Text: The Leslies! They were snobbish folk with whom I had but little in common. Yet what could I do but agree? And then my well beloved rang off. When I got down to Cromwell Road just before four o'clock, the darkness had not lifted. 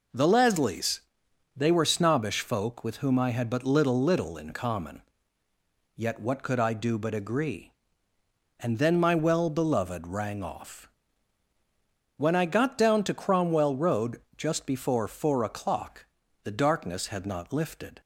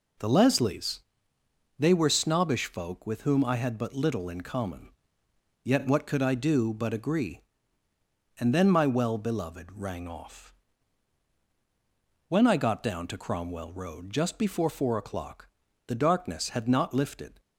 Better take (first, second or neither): second